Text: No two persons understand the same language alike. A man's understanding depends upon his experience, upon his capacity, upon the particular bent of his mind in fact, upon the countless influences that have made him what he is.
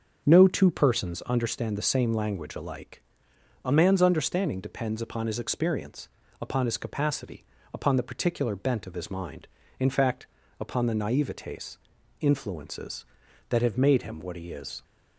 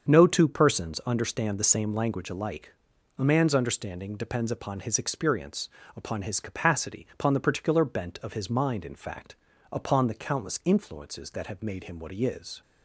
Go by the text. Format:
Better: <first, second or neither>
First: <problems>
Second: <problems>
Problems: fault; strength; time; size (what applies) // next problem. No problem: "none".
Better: second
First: starts louder than the rest; until 1.2 s; 6.5 dB // says "naivetes" for "countless"; at 10.9 s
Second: starts louder than the rest; until 1.1 s; 7 dB